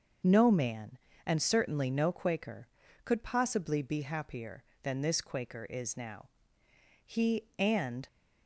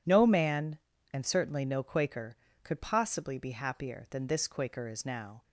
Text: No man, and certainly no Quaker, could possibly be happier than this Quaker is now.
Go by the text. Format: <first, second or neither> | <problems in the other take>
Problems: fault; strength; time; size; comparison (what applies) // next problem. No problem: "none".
second | starts louder than the rest; noticeable; until 1.5 s; 6 dB // goes on to say "He and"; noticeable; from 7.0 s on; 1.0 s long